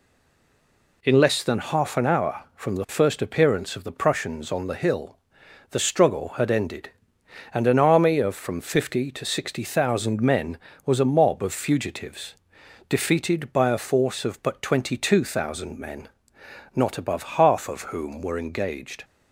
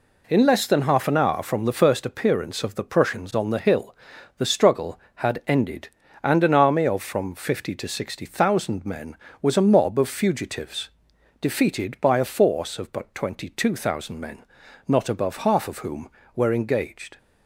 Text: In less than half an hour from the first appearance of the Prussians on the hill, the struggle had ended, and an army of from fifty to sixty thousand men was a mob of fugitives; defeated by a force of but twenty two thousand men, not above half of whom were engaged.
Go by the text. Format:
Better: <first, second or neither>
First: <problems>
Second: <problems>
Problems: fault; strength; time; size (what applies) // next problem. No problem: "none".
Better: second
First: stays silent before the first word; until 1.0 s; 1.0 s long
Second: none